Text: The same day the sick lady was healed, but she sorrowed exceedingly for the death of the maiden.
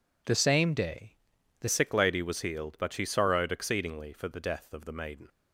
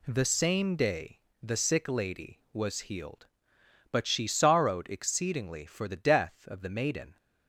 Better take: second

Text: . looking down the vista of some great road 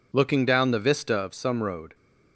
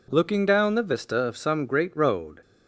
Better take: second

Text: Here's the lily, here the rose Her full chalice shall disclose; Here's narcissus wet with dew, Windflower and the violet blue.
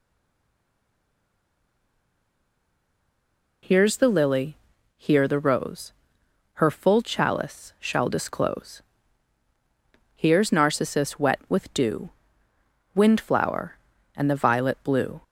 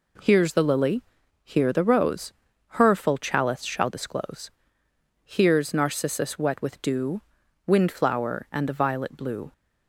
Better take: second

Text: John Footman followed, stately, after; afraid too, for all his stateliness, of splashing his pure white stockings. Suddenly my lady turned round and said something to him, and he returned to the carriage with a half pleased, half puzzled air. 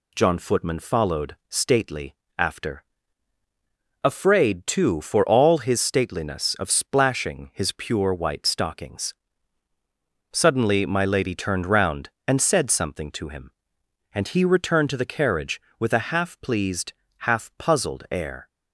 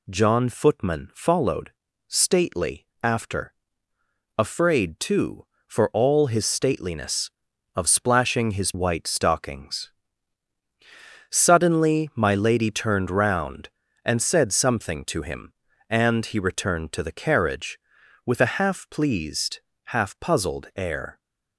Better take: first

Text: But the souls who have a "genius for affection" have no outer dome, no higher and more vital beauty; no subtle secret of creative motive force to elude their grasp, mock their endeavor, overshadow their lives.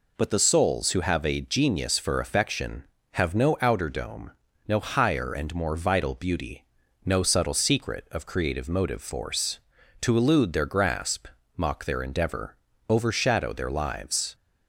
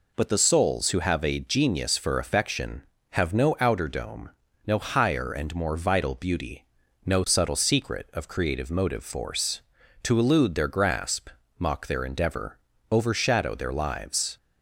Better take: neither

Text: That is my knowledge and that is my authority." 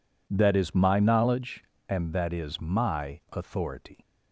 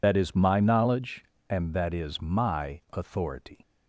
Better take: first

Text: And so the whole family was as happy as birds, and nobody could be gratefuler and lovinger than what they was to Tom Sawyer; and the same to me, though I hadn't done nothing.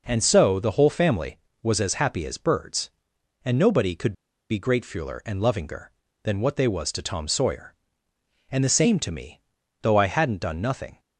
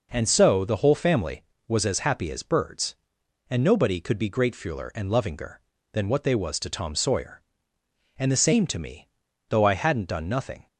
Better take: second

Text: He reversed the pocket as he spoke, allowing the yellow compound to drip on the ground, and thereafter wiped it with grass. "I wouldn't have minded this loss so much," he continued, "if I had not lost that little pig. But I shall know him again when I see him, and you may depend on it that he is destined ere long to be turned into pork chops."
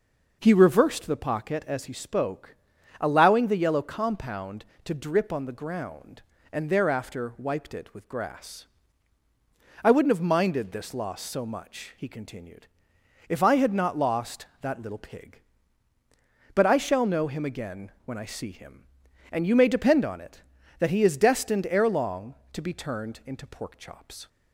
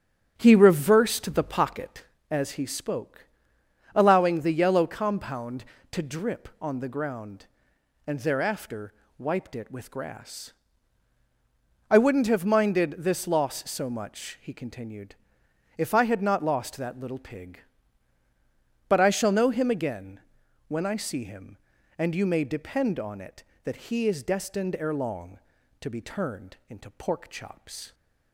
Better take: first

